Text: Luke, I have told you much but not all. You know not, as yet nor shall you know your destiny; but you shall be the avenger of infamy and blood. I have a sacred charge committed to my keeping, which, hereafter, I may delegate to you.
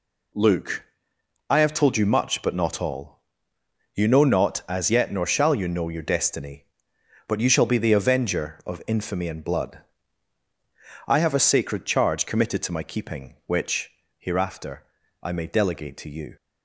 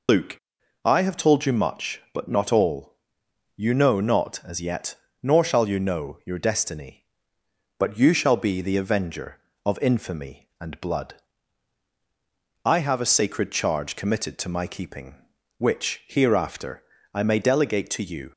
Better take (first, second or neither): first